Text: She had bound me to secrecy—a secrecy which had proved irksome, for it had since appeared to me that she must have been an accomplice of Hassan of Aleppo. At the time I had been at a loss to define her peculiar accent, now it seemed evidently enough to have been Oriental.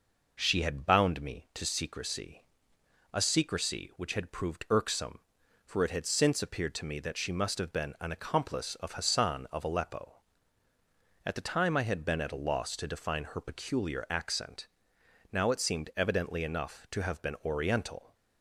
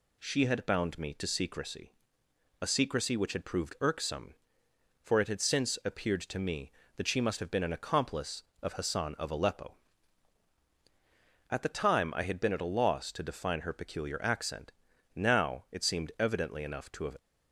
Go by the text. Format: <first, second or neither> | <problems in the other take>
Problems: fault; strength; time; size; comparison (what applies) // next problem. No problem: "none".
first | stops before "been Oriental"; at 17.1 s